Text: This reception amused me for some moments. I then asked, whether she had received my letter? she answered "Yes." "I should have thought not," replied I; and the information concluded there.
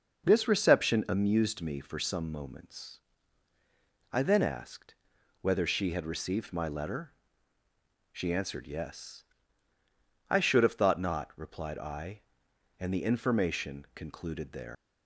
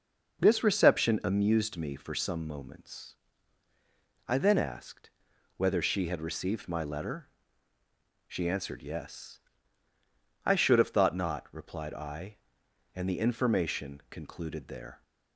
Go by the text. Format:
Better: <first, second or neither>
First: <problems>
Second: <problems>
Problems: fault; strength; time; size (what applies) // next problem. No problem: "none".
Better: second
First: leaves "there" unfinished; at 14.7 s; 115 ms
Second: none